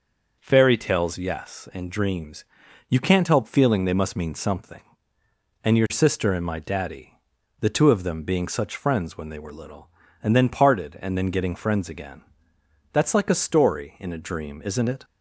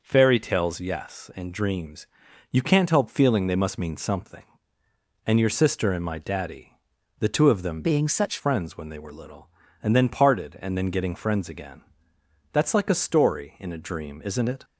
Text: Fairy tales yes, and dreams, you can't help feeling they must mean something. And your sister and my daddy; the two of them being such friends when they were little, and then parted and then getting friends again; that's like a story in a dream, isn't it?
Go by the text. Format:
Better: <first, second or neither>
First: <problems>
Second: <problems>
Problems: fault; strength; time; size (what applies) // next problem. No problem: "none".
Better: first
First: none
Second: changes voice from "being" to "such"; from 7.8 to 8.3 s; 0.5 s long